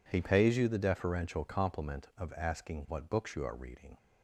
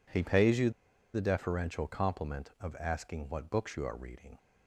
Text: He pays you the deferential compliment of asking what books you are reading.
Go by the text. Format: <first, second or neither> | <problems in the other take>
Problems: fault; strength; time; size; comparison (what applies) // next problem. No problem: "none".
first | pauses between "you" and "the"; at 0.7 s; 0.43 s long